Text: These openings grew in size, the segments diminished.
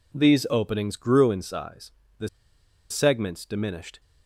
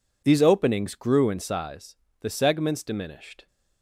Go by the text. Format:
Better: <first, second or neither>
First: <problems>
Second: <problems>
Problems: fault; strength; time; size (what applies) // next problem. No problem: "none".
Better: second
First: pauses between "the" and "segments"; noticeable; at 2.2 s; 0.61 s long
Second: none